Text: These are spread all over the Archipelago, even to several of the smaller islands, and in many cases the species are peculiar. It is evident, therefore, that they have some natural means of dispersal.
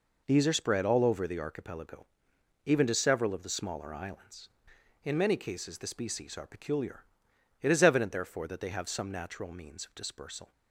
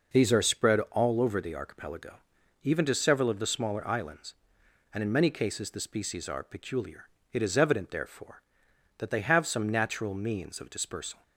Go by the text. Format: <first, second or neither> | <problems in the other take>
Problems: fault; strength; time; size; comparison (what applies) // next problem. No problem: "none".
second | skips "and"; at 4.7 s